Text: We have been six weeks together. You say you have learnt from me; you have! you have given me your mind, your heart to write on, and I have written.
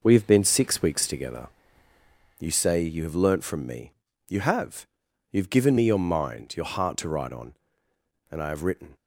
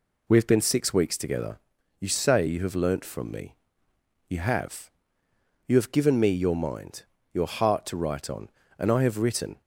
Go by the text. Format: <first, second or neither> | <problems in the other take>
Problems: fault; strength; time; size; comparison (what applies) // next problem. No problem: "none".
neither | none